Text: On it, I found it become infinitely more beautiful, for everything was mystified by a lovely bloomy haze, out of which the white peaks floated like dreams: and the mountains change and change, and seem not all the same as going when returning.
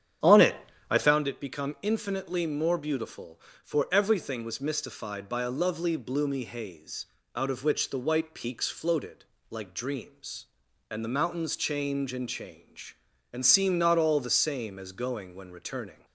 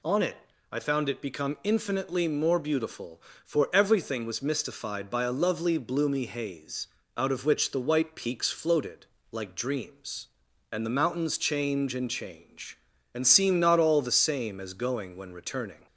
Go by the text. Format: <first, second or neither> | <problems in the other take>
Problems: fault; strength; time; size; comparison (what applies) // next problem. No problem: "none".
second | starts louder than the rest; strong; until 1.2 s; 9 dB // pauses between "floated" and "like"; slight; at 9.2 s; 0.24 s long; slight in the second